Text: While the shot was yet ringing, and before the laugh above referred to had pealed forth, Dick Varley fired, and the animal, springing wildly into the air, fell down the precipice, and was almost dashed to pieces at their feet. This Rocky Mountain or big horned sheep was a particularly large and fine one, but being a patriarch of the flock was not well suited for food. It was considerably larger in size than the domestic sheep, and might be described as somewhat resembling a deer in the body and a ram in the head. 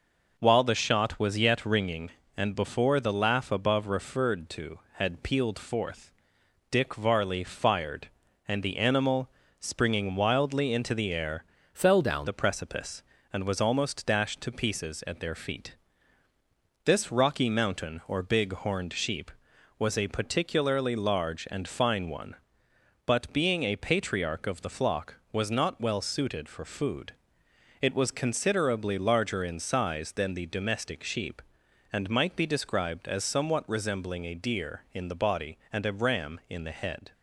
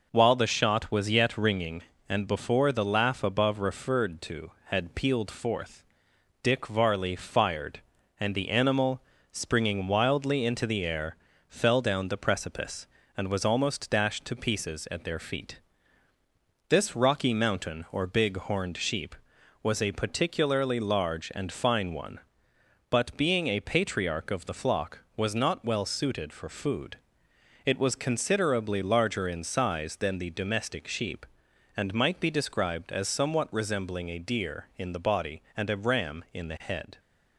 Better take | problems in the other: second | changes voice from "fell" to "down"; from 11.7 to 12.2 s; 0.5 s long

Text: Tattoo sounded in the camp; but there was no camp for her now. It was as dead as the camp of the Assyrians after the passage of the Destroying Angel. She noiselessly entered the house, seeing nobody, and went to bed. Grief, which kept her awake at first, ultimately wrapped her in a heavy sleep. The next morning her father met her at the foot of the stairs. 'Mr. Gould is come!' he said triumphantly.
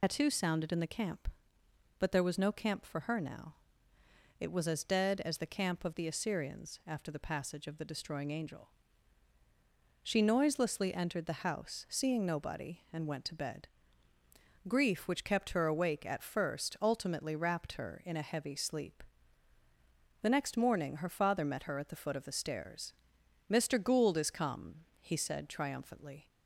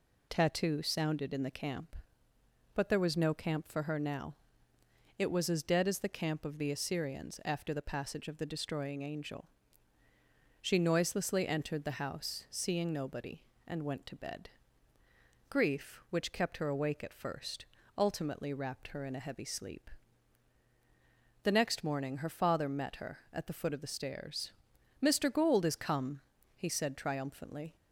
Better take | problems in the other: second | loses the start of "Tattoo"; at 0.0 s; 105 ms

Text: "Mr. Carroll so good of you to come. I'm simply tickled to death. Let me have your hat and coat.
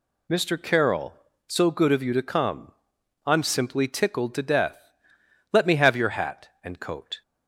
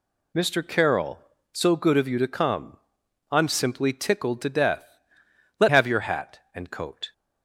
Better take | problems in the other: first | skips "me"; at 5.6 s

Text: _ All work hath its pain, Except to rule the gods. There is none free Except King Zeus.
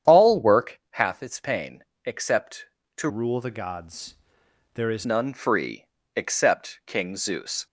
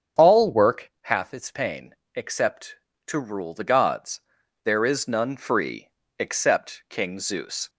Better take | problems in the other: second | starts louder than the rest; strong; until 1.1 s; 9 dB; strong in the second // changes voice from "rule" to "is"; from 3.0 to 5.0 s; 2.0 s long // pauses between "free" and "Except"; slight; at 5.8 s; 0.28 s long; slight in the second

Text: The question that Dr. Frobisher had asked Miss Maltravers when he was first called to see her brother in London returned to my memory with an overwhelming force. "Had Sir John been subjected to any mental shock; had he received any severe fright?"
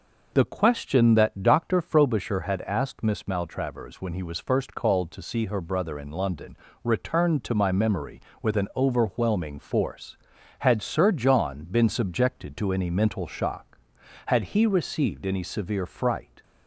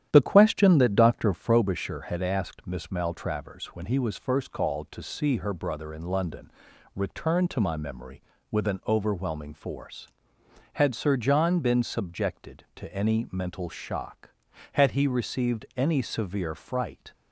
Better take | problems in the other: first | starts louder than the rest; strong; until 1.7 s; 10.5 dB // pauses between "London" and "returned"; noticeable; at 6.5 s; 0.46 s long; slight in the first

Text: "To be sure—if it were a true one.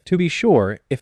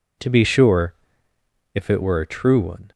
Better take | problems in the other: second | stops before "it were a true one"; at 0.9 s

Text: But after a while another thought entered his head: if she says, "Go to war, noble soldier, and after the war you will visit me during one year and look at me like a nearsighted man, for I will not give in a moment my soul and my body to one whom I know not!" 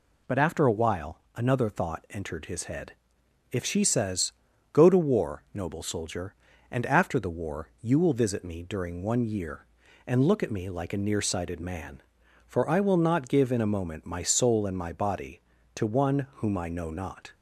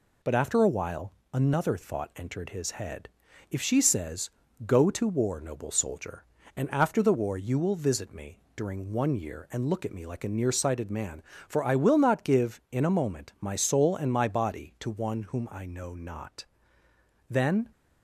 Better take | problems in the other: first | pauses between "while" and "another"; slight; at 1.1 s; 0.20 s long; slight in the first // goes on to say "Then"; slight; from 17.2 s on; 0.40 s long

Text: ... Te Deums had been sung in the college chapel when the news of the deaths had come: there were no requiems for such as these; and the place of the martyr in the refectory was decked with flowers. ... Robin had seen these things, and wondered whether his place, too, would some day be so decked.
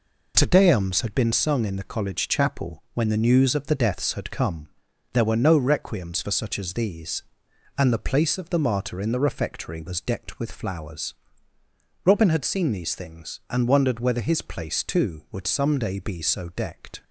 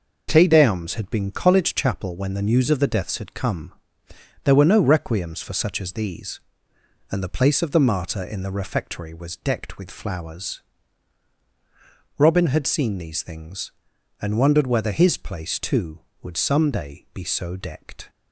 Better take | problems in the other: first | skips "sung in the"; at 1.3 s

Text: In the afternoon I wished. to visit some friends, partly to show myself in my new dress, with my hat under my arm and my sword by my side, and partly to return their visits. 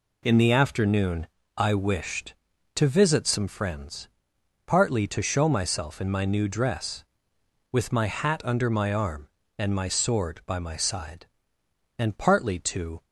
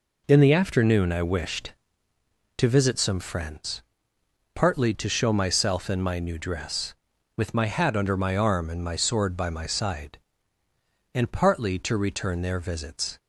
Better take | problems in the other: second | pauses between "afternoon" and "I"; slight; at 1.2 s; 0.32 s long // stops before "return their visits"; at 13.0 s

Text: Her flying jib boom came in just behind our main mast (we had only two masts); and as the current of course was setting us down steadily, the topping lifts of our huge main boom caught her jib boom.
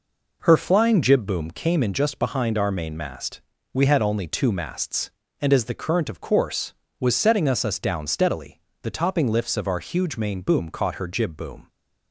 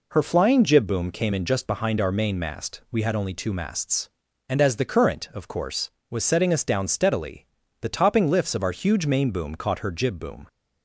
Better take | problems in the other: second | says "us" twice; at 7.6 s

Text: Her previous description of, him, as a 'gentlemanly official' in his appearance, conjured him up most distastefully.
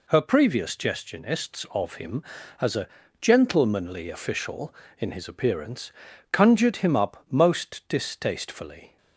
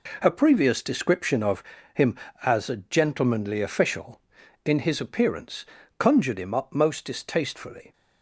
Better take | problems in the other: second | says "gestionists" for "description"; at 0.7 s // pauses between "a" and "gentlemanly"; slight; at 2.8 s; 0.34 s long

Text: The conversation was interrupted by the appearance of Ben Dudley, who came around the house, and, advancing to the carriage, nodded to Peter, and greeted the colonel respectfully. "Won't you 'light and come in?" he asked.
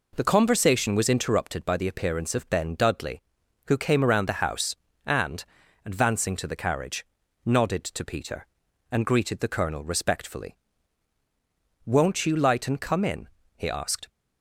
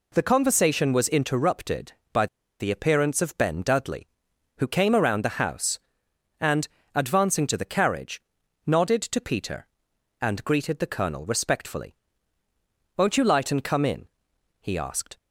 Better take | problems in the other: first | pauses between "by" and "the"; slight; at 2.2 s; 0.32 s long

